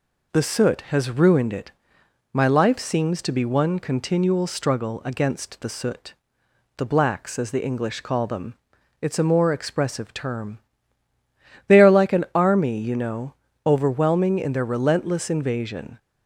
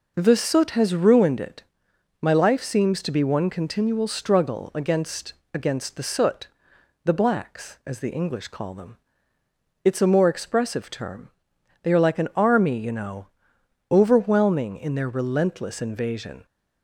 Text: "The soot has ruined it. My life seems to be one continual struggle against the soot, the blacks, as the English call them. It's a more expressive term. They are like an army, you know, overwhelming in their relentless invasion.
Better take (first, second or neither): first